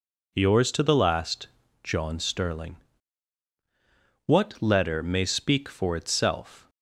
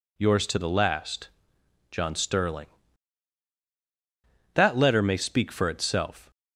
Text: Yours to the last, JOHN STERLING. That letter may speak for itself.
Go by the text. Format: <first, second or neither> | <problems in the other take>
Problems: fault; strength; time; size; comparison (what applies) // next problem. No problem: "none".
second | says "What" for "That"; at 4.2 s